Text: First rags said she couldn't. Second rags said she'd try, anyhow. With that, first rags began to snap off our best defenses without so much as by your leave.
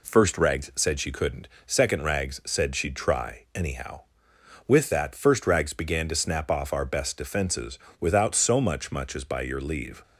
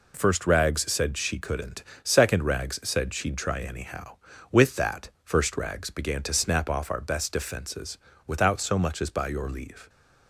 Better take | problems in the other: second | pauses between "defenses" and "without"; slight; at 7.7 s; 0.20 s long; slight in the second // says "much" twice; at 8.9 s

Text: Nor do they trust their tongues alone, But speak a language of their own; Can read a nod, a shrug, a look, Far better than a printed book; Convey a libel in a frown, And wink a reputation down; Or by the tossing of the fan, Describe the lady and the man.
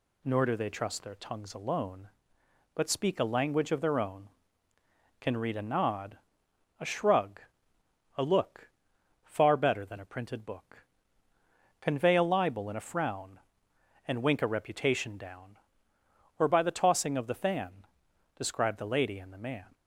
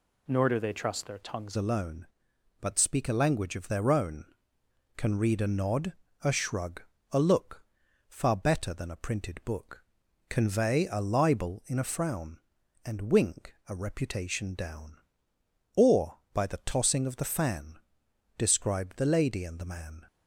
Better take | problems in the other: first | changes voice at "alone"; from 1.5 s on; 18.5 s long

